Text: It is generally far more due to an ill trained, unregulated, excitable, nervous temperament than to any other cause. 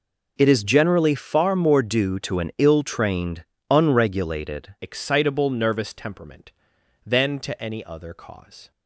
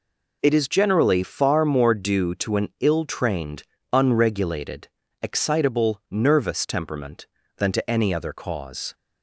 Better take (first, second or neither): second